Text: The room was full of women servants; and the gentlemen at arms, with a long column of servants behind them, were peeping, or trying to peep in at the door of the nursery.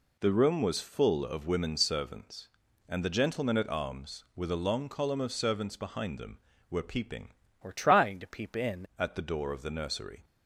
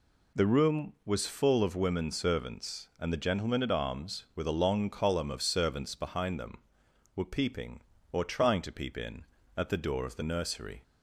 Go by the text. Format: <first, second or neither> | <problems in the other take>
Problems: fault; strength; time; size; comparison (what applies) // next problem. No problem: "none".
second | changes voice from "or" to "in"; from 7.6 to 8.8 s; 1.2 s long